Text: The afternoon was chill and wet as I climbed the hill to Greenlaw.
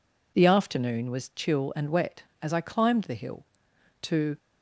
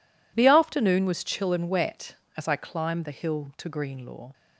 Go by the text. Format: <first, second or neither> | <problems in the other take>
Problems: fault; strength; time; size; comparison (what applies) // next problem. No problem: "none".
second | stops before "Greenlaw"; at 4.3 s